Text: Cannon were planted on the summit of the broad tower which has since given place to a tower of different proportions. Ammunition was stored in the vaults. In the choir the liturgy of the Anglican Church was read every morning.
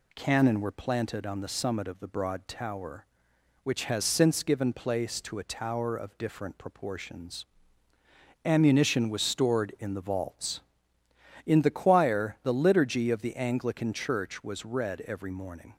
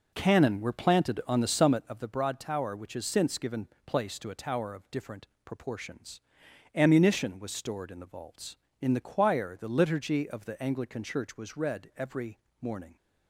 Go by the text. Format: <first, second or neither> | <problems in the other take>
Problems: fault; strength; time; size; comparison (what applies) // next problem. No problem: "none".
first | starts louder than the rest; noticeable; until 1.9 s; 5 dB // pauses between "given" and "place"; slight; at 3.6 s; 0.20 s long // pauses between "different" and "proportions"; slight; at 5.2 s; 0.18 s long // pauses between "every" and "morning"; slight; at 12.3 s; 0.22 s long